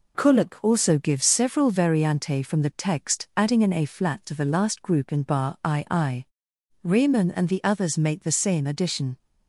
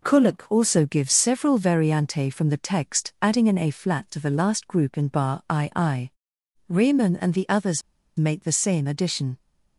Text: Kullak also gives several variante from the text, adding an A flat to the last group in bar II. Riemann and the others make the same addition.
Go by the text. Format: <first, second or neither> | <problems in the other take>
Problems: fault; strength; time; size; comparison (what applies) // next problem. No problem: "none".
first | pauses between "others" and "make"; slight; at 7.8 s; 0.35 s long